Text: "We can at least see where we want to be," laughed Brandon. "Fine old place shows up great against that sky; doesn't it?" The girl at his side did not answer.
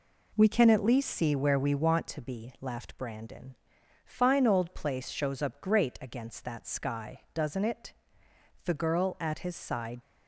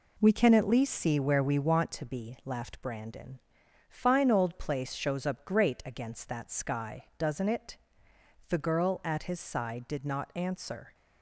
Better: second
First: stops before "did not answer"; at 10.0 s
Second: none

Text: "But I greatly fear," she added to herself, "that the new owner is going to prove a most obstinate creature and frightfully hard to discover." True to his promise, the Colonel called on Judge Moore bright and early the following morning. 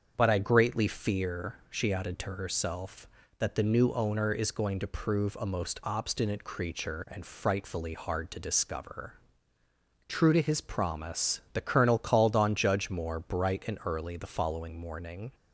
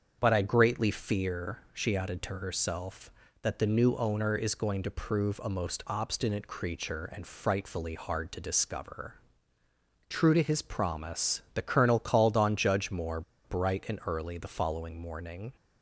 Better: first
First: starts louder than the rest; strong; until 1.1 s; 7 dB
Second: starts louder than the rest; strong; until 1.2 s; 7 dB // pauses between "Moore" and "bright"; slight; at 13.2 s; 0.23 s long

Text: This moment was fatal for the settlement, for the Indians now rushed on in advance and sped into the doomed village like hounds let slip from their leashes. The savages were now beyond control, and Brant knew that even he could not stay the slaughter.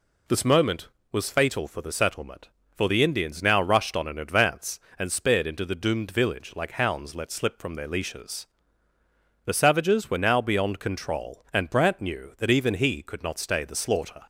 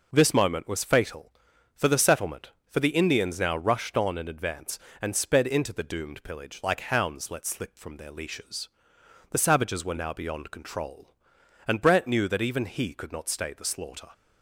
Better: first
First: none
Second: says "pillage" for "village"; at 6.2 s

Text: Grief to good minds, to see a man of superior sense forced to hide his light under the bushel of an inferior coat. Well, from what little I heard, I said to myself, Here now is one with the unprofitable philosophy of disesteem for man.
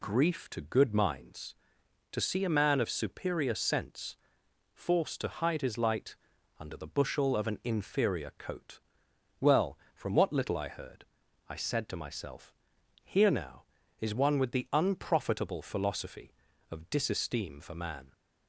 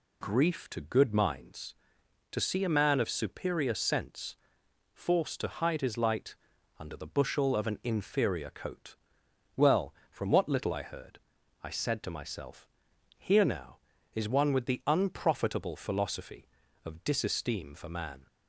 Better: neither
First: pauses between "sense" and "forced"; noticeable; at 4.1 s; 0.58 s long // pauses between "light" and "under"; at 6.1 s; 0.42 s long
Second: pauses between "sense" and "forced"; noticeable; at 4.3 s; 0.58 s long // pauses between "light" and "under"; at 6.3 s; 0.42 s long

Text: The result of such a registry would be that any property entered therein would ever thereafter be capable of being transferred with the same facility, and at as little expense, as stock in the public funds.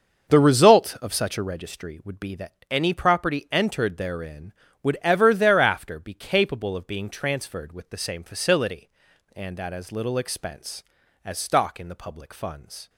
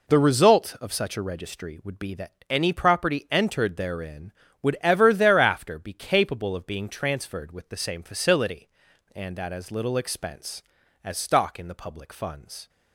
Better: second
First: starts louder than the rest; until 1.6 s; 6 dB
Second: none

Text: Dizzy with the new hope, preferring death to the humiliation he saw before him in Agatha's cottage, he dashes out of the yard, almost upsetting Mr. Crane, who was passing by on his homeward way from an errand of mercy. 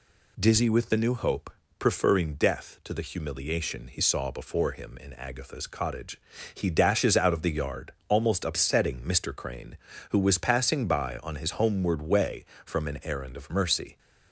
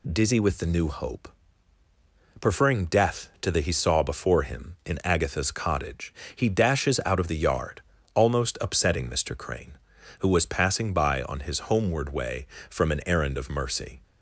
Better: first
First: none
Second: skips "humiliation"; at 3.5 s

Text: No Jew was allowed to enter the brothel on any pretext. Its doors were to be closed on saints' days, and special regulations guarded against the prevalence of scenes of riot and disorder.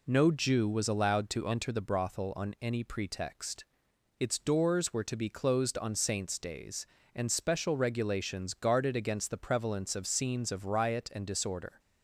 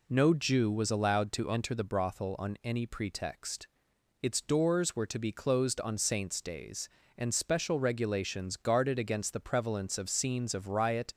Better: first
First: none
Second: stops before "and disorder"; at 11.1 s

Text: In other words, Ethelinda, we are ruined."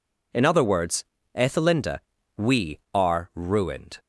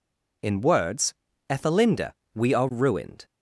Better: first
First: none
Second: skips "other"; at 0.5 s

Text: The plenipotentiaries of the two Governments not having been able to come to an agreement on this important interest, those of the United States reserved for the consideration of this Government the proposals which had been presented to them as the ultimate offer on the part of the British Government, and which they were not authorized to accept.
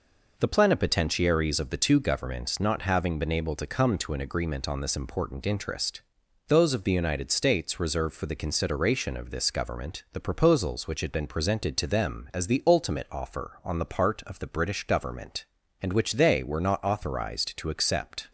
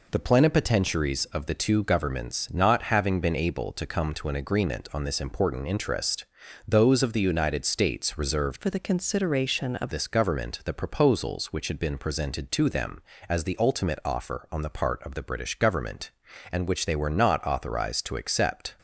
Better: first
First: none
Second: changes voice from "for" to "of"; from 8.5 to 9.9 s; 1.4 s long

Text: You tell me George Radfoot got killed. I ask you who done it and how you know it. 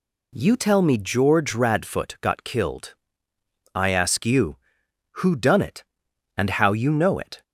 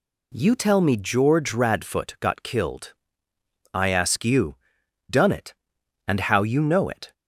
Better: first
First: none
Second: skips "who"; at 4.8 s

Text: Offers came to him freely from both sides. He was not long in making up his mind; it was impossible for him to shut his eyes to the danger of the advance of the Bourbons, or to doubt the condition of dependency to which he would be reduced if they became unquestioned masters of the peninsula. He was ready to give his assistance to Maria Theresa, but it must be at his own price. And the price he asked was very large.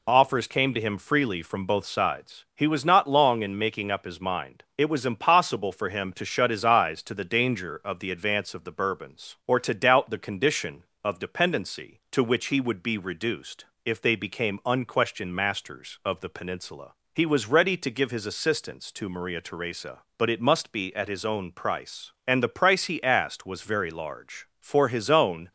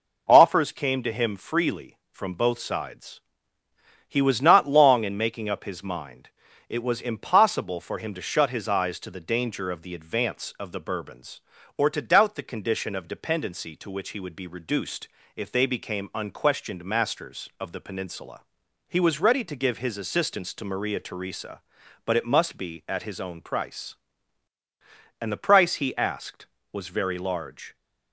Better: second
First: pauses between "reduced" and "if"; slight; at 13.6 s; 0.18 s long // goes on to say "For his own"; noticeable; from 24.5 s on; 0.92 s long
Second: pauses between "reduced" and "if"; slight; at 15.0 s; 0.26 s long

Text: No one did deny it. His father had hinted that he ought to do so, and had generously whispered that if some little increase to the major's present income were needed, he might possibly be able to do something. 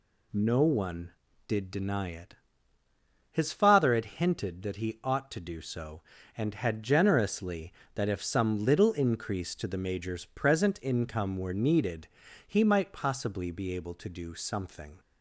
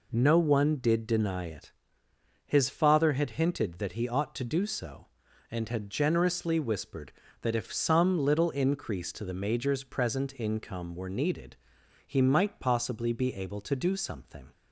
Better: second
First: skips "whispered"; at 7.8 s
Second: none

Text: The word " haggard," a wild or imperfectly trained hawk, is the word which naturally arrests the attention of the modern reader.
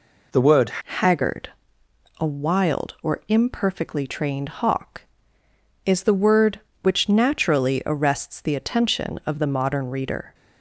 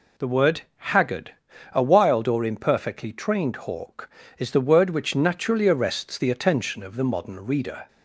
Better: second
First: changes voice at "haggard"; from 0.7 s on; 9.6 s long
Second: none

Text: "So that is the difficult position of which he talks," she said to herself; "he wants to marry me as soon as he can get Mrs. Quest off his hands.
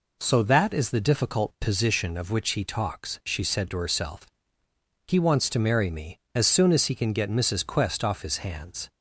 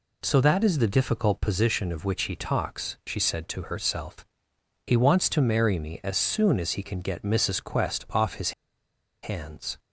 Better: first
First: none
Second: pauses between "his" and "hands"; noticeable; at 8.5 s; 0.71 s long

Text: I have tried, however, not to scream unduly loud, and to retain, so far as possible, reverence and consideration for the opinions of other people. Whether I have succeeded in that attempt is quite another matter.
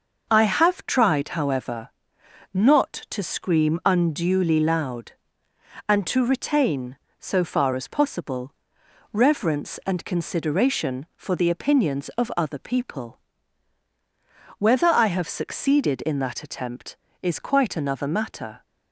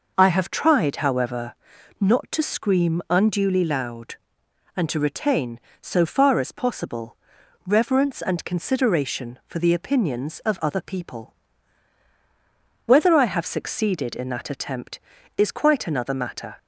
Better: neither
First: none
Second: none

